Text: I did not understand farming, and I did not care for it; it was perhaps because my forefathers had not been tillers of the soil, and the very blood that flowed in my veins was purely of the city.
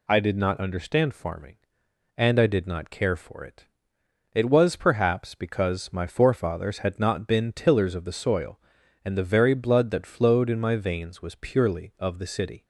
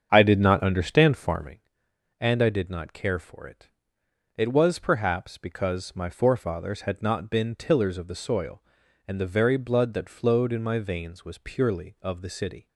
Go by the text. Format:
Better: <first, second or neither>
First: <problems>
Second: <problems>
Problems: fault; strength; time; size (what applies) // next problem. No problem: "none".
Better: first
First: none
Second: starts louder than the rest; strong; until 1.6 s; 7.5 dB